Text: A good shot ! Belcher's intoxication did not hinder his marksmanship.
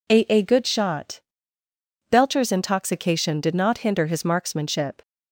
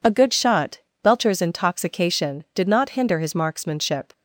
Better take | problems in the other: second | says "A" twice; at 0.2 s

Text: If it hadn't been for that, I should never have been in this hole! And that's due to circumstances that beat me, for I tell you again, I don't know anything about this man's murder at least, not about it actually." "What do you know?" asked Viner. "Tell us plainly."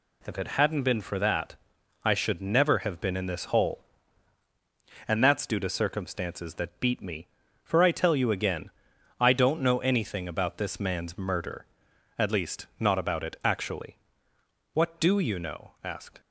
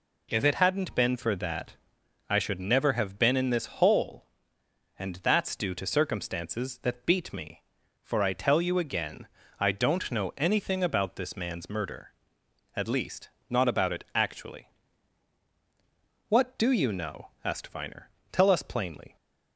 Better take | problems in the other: second | stops before "Viner Tell us plainly"; at 16.1 s

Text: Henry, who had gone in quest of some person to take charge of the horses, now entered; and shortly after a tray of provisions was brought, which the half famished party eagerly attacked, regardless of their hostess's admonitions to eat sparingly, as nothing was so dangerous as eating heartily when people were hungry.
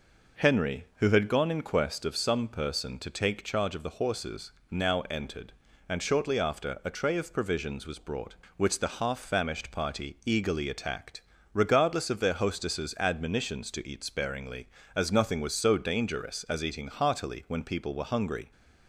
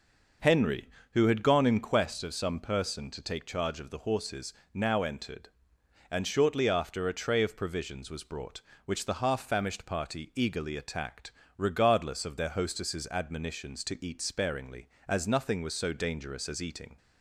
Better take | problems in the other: first | stops before "heartily when people were hungry"; at 16.9 s

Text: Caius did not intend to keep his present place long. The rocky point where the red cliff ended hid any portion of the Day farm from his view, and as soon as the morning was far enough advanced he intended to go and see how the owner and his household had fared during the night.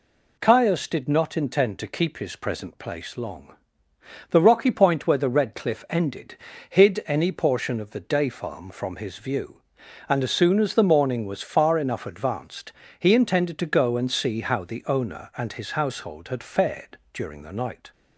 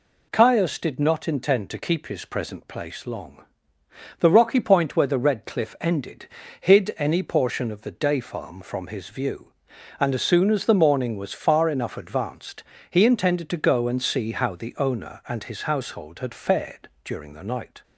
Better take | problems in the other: neither | pauses between "ended" and "hid"; slight; the same in both // pauses between "advanced" and "he"; slight; the same in both // pauses between "fared" and "during"; slight; the same in both

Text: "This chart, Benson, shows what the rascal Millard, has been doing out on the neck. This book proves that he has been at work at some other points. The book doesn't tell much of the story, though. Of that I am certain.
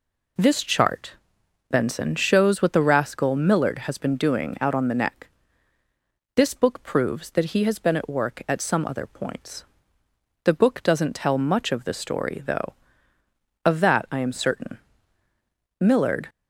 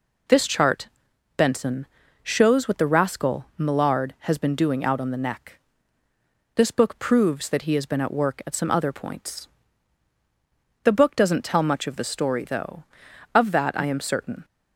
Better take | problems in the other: second | goes on to say "Millard"; slight; from 15.8 s on; 0.48 s long

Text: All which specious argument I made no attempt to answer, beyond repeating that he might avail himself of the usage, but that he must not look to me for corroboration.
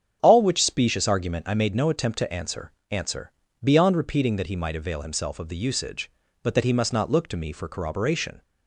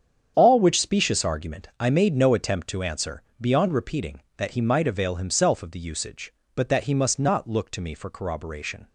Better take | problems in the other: second | starts louder than the rest; strong; until 1.2 s; 8 dB; strong in the second // says "answer" twice; at 2.8 s

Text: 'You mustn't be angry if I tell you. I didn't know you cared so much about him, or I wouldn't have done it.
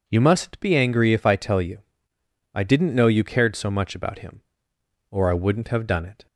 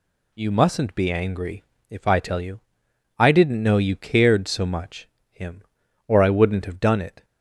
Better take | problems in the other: first | pauses between "angry" and "if"; slight; at 1.6 s; 0.24 s long // skips "about"; at 5.1 s

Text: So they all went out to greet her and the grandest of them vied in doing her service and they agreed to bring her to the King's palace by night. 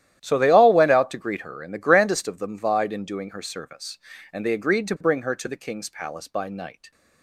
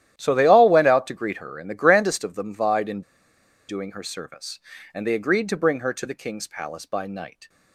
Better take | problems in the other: first | starts louder than the rest; strong; until 1.2 s; 12 dB; strong in the first // pauses between "in" and "doing"; noticeable; at 3.0 s; 0.67 s long

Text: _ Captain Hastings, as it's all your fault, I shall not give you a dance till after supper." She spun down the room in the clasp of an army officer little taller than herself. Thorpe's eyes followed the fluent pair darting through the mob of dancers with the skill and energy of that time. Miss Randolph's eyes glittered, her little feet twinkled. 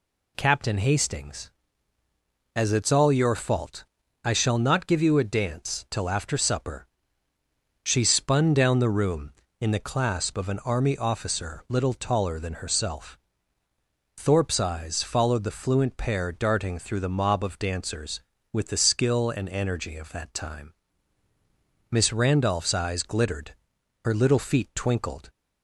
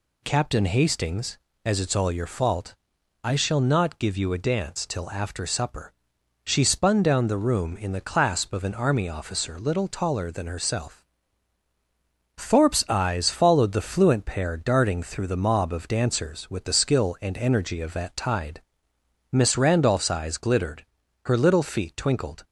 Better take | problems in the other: first | says "tide" for "time"; at 18.1 s

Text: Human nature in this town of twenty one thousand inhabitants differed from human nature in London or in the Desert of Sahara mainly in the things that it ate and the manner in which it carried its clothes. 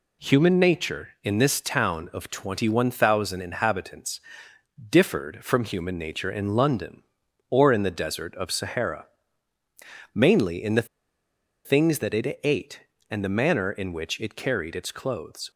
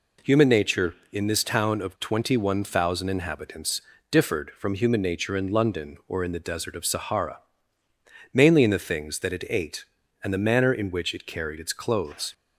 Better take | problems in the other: second | pauses between "inhabitants" and "differed"; noticeable; at 4.1 s; 0.70 s long; slight in the second // pauses between "Sahara" and "mainly"; at 9.0 s; 1.0 s long; noticeable in the second // pauses between "the" and "things"; noticeable; at 10.8 s; 0.78 s long

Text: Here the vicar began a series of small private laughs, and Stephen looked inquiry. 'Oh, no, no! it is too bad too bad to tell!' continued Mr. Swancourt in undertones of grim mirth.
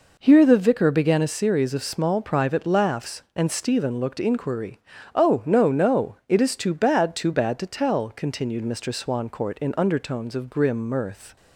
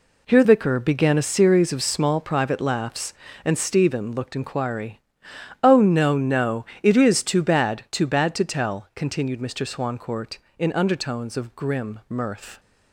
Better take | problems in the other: first | skips "the"; at 0.4 s

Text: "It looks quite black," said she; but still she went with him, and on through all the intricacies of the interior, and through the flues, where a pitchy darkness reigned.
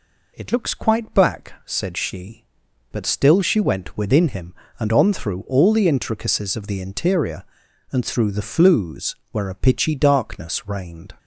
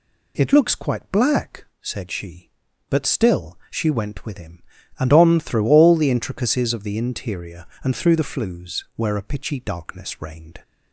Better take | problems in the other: second | says "within" for "with"; at 3.9 s

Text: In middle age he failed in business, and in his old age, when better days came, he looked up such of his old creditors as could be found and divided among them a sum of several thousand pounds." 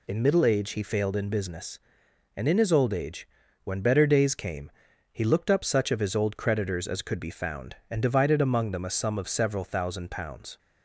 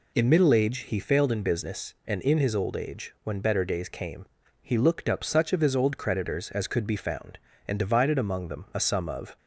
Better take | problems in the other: first | stops before "several thousand pounds"; at 9.3 s

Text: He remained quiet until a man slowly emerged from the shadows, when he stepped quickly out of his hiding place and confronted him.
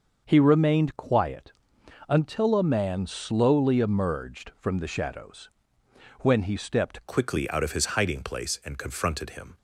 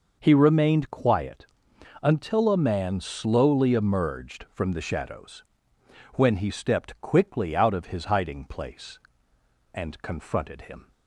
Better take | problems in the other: second | starts louder than the rest; until 1.2 s; 6 dB // pauses between "quiet" and "until"; noticeable; at 1.5 s; 0.56 s long; noticeable in the second // changes voice at "quickly"; from 7.0 s on; 2.5 s long

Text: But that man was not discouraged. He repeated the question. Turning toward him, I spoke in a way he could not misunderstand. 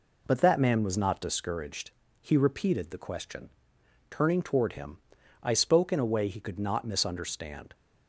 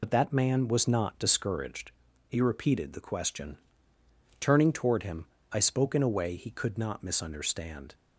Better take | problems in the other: first | loses the start of "But"; at 0.0 s; 50 ms

